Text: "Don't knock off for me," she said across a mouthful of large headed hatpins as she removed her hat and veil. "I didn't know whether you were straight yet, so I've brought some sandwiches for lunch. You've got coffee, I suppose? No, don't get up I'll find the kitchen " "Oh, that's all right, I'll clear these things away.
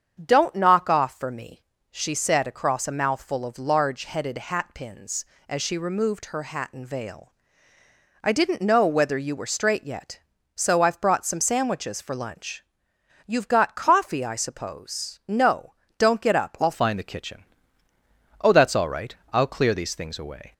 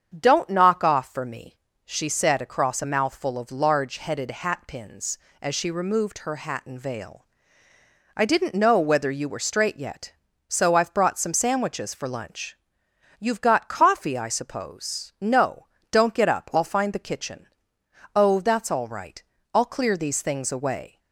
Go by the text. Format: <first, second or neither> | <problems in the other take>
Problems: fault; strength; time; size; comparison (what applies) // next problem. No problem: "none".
second | starts louder than the rest; strong; until 1.2 s; 7.5 dB; strong in the second // changes voice at "find"; from 16.7 s on; 3.8 s long